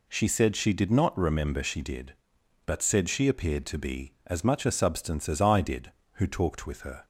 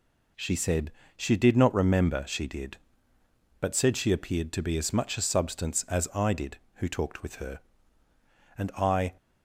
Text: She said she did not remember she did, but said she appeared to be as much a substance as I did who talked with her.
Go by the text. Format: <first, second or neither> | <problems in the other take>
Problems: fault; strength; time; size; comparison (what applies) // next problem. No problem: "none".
first | pauses between "said" and "she"; slight; at 0.9 s; 0.24 s long // goes on to say "And I"; from 8.5 s on; 0.58 s long